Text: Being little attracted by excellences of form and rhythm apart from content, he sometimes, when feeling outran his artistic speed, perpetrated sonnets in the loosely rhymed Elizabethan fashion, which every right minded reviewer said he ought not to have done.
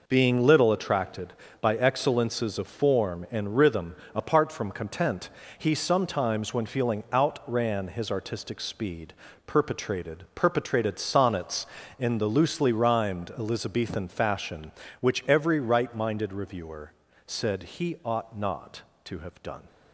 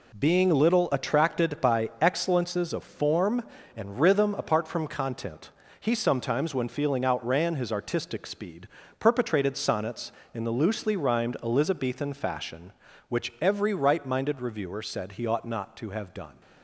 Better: second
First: pauses between "rhythm" and "apart"; slight; at 3.9 s; 0.18 s long // says "perpetrated" twice; at 10.3 s // pauses between "reviewer" and "said"; slight; at 16.9 s; 0.34 s long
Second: none

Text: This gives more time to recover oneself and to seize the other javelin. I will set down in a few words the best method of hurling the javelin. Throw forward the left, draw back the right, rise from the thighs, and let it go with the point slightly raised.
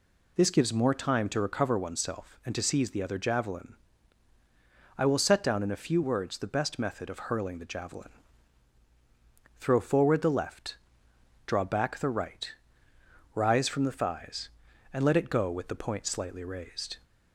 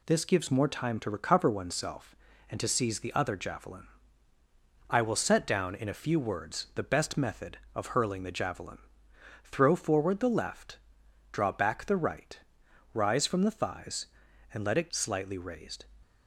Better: first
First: none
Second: skips "go with the point"; at 14.8 s

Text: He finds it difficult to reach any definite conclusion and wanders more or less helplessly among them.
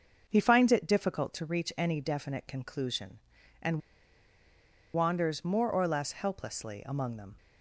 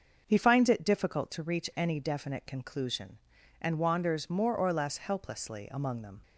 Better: second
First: starts louder than the rest; noticeable; until 1.2 s; 6 dB // pauses between "and" and "wanders"; at 3.7 s; 1.1 s long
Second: starts louder than the rest; noticeable; until 1.2 s; 6 dB

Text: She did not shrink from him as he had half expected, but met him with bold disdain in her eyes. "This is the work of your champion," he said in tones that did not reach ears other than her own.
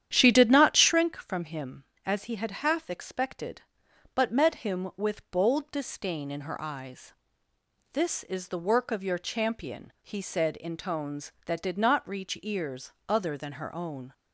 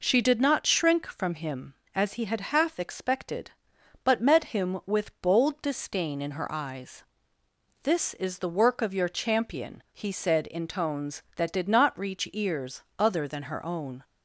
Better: second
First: starts louder than the rest; strong; until 1.0 s; 10 dB // pauses between "ears" and "other"; slight; at 12.9 s; 0.16 s long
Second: pauses between "ears" and "other"; slight; at 12.8 s; 0.16 s long

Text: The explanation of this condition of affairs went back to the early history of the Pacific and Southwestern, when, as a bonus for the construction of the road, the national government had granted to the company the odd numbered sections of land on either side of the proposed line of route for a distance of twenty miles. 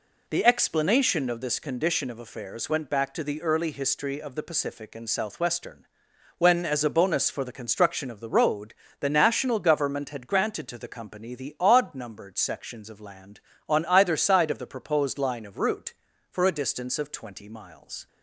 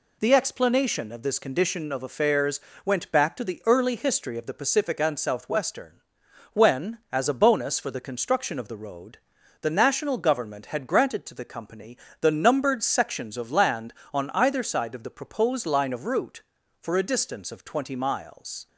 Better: first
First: none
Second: pauses between "affairs" and "went"; slight; at 2.5 s; 0.26 s long // pauses between "company" and "the"; slight; at 11.9 s; 0.24 s long // skips "odd"; at 12.3 s

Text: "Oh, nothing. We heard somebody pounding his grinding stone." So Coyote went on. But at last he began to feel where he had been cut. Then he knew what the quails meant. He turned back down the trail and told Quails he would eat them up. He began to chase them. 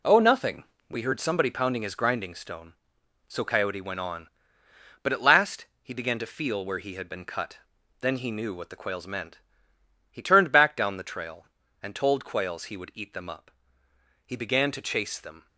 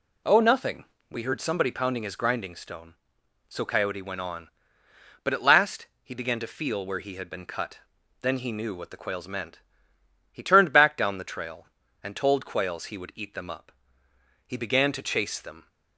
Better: second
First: gets quieter; strong; throughout; 7.5 dB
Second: none

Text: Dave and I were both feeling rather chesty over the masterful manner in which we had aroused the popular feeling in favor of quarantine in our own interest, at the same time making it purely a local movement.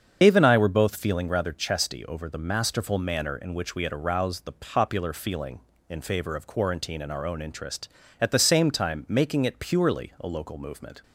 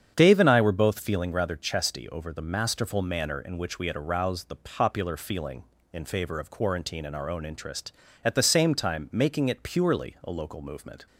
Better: second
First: loses the start of "Dave"; at 0.2 s; 85 ms // starts louder than the rest; strong; until 1.2 s; 7.5 dB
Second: starts louder than the rest; strong; until 1.1 s; 8 dB

